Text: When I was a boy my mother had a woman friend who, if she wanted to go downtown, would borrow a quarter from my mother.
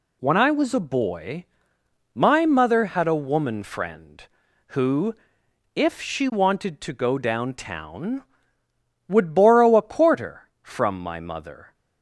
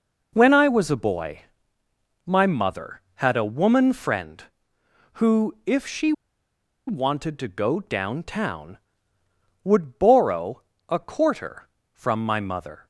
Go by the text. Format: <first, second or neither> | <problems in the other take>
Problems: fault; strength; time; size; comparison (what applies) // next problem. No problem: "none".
first | pauses between "boy" and "my"; noticeable; at 1.4 s; 0.84 s long; noticeable in the first // pauses between "she" and "wanted"; noticeable; at 6.1 s; 0.75 s long // pauses between "borrow" and "a"; slight; at 10.6 s; 0.26 s long